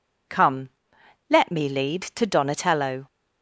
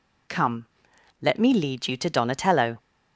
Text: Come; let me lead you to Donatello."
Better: second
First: skips "you"; at 2.0 s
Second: none

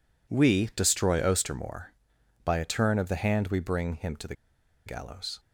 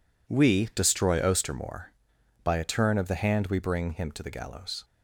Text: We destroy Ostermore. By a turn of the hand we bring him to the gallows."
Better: second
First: pauses between "the" and "gallows"; noticeable; at 4.3 s; 0.51 s long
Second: none

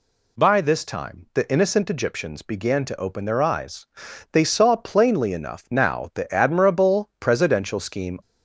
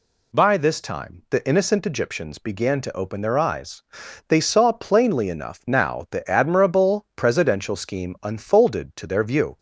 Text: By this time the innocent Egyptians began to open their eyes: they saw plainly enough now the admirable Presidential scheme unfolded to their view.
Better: second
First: stops before "unfolded to their view"; at 8.2 s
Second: none

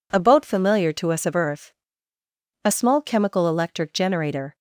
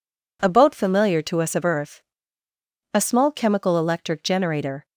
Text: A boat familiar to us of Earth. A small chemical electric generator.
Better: neither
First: none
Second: none

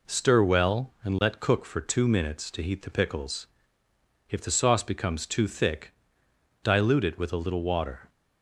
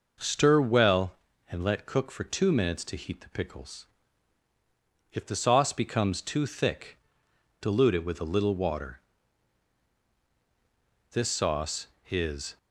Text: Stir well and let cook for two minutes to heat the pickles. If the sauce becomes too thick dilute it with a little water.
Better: first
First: pauses between "thick" and "dilute"; noticeable; at 5.9 s; 0.70 s long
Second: pauses between "thick" and "dilute"; noticeable; at 6.9 s; 0.64 s long // goes on to say "This sauce is"; from 11.1 s on; 1.4 s long

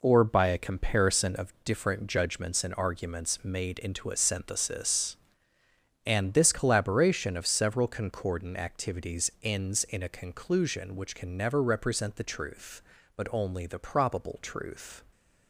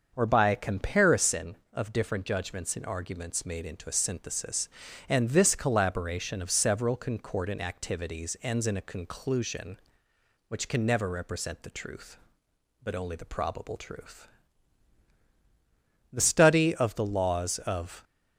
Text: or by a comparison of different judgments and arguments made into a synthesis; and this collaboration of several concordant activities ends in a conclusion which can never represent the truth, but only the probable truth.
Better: first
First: none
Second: starts louder than the rest; until 1.1 s; 6.5 dB // goes on to say "The study of the laws of"; strong; from 16.1 s on; 1.9 s long

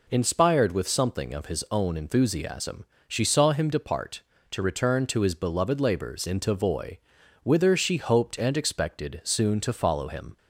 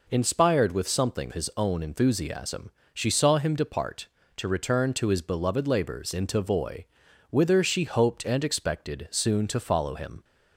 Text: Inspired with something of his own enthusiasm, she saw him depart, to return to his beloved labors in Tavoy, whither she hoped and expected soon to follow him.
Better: first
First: none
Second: skips "of"; at 1.3 s

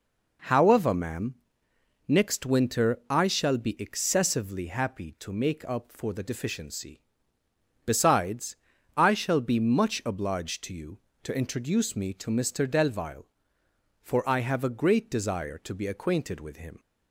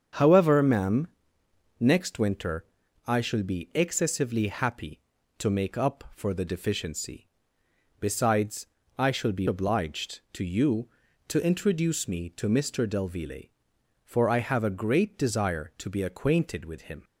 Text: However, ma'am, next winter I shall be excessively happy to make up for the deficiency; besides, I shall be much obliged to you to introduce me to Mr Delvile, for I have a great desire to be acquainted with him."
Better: first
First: none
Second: starts louder than the rest; strong; until 1.9 s; 7 dB // pauses between "winter" and "I"; at 2.6 s; 0.40 s long // skips "much"; at 9.4 s

